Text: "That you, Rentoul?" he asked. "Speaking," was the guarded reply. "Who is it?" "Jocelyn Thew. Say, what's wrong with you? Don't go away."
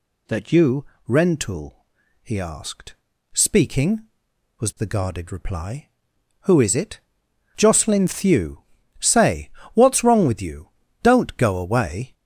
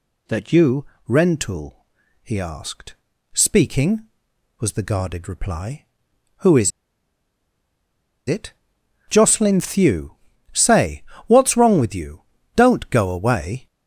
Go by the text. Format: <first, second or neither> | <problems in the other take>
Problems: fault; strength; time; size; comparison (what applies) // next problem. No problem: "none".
first | pauses between "is" and "it"; strong; at 6.7 s; 1.5 s long